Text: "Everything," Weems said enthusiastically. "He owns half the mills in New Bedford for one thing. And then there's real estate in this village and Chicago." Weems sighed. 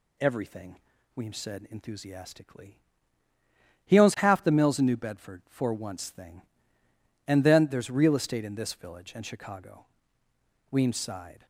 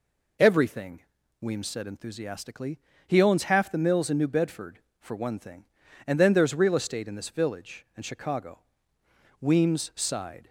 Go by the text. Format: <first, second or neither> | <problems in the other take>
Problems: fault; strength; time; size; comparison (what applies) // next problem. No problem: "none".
second | says "once" for "one"; at 5.7 s